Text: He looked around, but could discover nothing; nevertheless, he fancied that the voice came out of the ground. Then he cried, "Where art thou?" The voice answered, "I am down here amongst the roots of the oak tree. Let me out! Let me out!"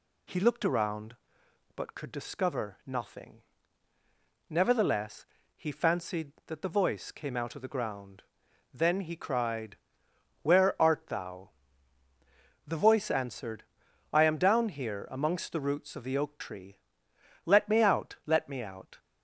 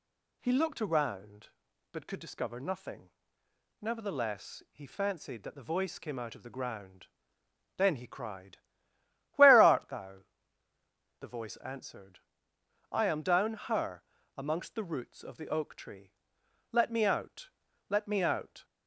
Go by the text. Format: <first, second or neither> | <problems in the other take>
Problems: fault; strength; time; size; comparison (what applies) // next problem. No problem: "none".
first | says "her" for "here"; at 13.5 s